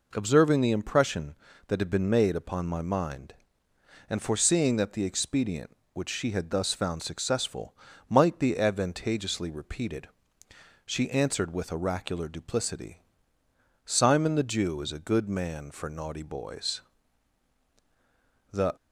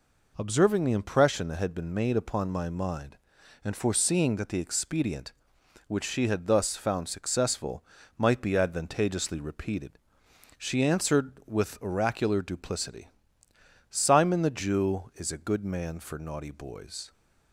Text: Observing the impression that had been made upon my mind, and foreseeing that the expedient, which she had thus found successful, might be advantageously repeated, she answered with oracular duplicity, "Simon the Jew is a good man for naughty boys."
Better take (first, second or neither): second